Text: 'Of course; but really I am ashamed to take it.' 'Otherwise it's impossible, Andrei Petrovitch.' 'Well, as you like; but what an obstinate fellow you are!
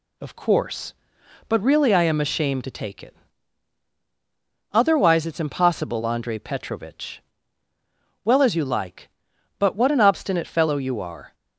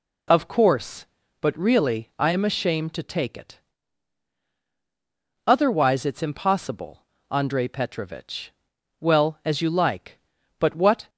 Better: first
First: none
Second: stops before "an obstinate fellow you are"; at 11.0 s

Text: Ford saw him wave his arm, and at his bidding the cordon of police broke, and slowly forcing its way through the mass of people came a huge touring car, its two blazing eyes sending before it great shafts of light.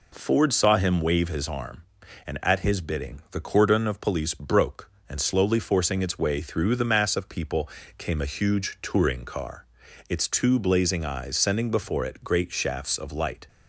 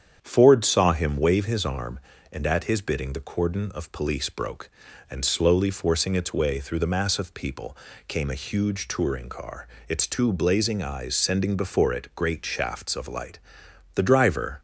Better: first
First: pauses between "people" and "came"; slight; at 7.6 s; 0.30 s long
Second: starts louder than the rest; strong; until 1.2 s; 8 dB // pauses between "people" and "came"; slight; at 7.7 s; 0.30 s long // goes on to say "The driver"; noticeable; from 13.9 s on; 0.66 s long

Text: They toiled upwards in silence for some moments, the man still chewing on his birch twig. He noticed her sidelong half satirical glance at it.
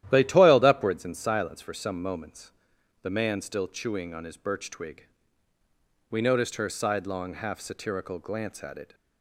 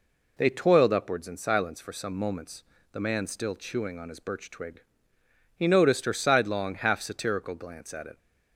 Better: second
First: starts louder than the rest; strong; until 1.1 s; 12.5 dB // says "We" for "He"; at 6.1 s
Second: none

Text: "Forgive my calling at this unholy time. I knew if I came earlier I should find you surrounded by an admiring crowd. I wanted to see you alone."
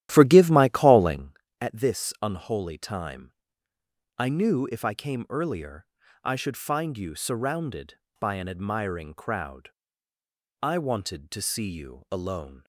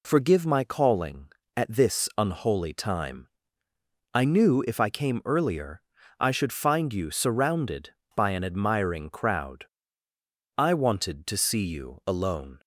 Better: second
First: starts louder than the rest; strong; until 1.4 s; 12.5 dB // pauses between "earlier" and "I"; at 5.8 s; 0.38 s long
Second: pauses between "earlier" and "I"; at 5.8 s; 0.38 s long

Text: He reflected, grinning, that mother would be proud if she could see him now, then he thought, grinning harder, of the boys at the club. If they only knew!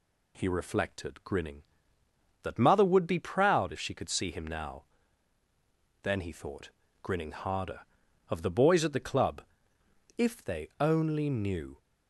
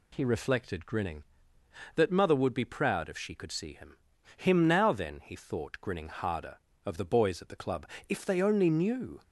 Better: first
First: none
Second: says "him" twice; at 4.3 s

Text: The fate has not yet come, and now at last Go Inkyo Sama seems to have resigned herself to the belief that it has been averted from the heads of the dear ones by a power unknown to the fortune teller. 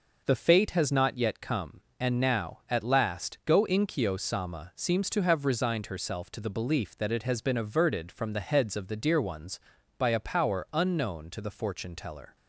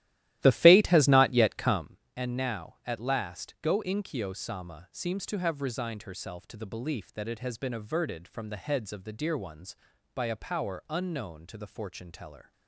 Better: first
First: none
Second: starts louder than the rest; strong; until 2.0 s; 14.5 dB

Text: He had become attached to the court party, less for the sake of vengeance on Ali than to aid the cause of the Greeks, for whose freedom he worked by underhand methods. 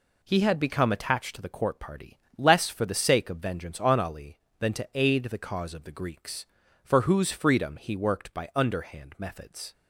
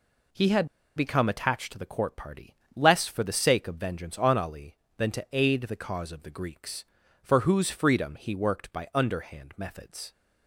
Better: first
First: none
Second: pauses between "had" and "become"; slight; at 0.6 s; 0.29 s long

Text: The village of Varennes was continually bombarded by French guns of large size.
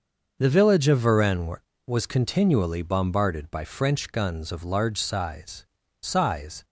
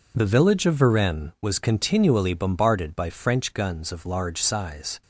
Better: second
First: starts louder than the rest; until 1.4 s; 6.5 dB // says "size" twice; at 5.9 s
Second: none

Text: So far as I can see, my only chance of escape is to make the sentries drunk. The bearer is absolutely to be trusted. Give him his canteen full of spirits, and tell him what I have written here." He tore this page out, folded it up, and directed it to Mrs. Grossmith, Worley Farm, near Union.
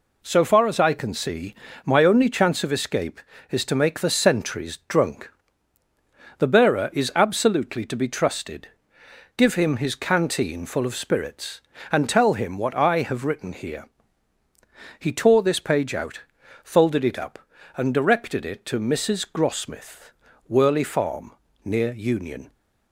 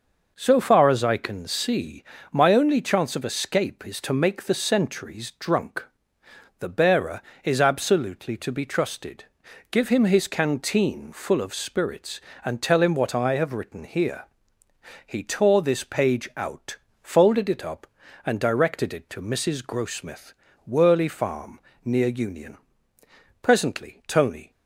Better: first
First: none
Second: goes on to say "Presently Tony"; noticeable; from 23.4 s on; 1.0 s long

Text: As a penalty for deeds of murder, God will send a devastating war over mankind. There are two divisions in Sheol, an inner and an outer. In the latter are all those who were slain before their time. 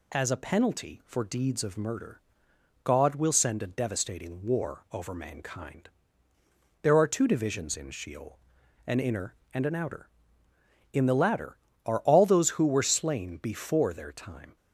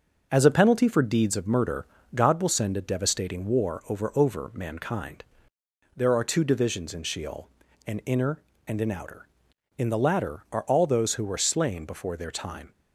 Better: first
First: none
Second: says "over" twice; at 4.1 s

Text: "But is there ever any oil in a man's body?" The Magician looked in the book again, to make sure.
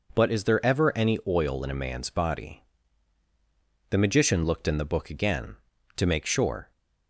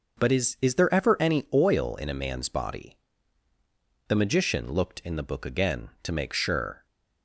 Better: first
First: none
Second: says "is" twice; at 0.5 s

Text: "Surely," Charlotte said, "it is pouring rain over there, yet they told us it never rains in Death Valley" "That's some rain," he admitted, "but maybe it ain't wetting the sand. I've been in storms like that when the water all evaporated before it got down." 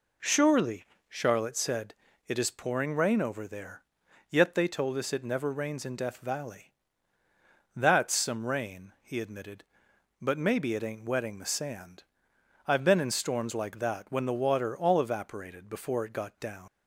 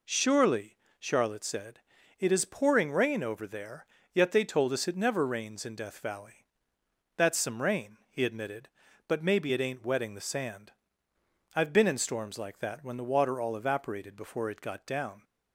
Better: second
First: pauses between "Valley" and "That's"; at 6.7 s; 1.0 s long // leaves "down" unfinished; at 16.6 s; 100 ms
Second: pauses between "Valley" and "That's"; noticeable; at 6.4 s; 0.70 s long

